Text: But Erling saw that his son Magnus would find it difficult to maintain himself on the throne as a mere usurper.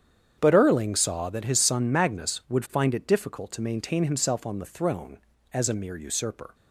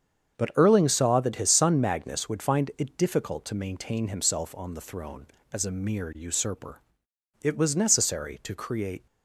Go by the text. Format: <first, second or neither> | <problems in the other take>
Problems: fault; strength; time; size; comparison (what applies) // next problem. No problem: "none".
first | starts louder than the rest; strong; until 1.4 s; 7 dB; strong in the first // goes on to say "It was necessary to create"; from 7.4 s on; 1.6 s long